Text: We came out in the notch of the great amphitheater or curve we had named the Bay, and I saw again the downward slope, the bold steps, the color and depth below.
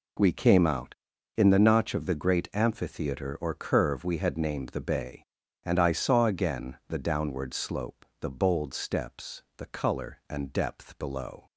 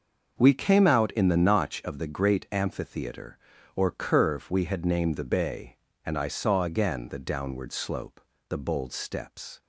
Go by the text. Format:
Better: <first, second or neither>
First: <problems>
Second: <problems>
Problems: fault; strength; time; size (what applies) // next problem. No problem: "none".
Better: first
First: none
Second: starts louder than the rest; until 1.4 s; 6.5 dB // stops before "the color and depth below"; at 9.6 s